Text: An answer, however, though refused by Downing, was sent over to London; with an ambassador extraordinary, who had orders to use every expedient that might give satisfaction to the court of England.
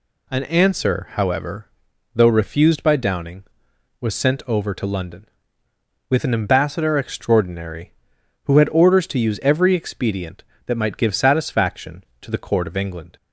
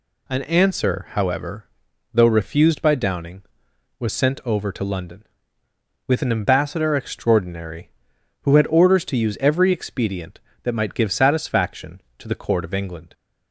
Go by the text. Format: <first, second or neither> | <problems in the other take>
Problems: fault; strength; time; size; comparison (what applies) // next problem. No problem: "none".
neither | none